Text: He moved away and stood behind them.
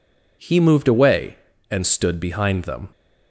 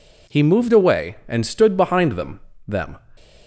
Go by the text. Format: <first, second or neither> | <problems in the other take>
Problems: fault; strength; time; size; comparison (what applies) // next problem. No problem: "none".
first | says "them" twice; at 2.6 s